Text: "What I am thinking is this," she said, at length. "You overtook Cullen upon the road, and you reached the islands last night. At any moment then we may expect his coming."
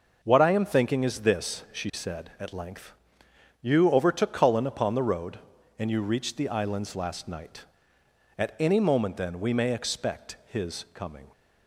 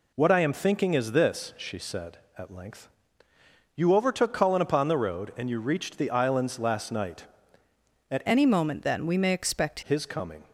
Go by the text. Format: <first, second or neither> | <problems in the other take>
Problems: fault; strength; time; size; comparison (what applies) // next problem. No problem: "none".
first | changes voice from "any" to "expect"; from 8.2 to 9.7 s; 1.5 s long